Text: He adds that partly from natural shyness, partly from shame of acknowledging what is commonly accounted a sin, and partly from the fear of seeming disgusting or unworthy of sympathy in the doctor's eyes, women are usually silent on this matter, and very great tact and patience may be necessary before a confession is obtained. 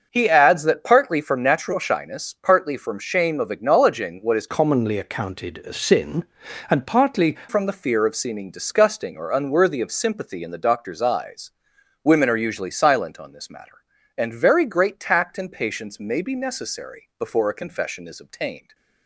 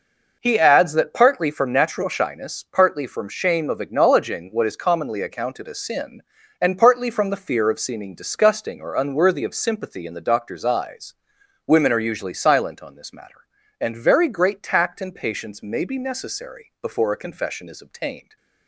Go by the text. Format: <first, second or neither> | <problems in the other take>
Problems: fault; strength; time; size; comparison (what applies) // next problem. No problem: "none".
second | starts louder than the rest; noticeable; until 1.1 s; 6 dB // changes voice from "commonly" to "partly"; from 4.4 to 7.3 s; 2.9 s long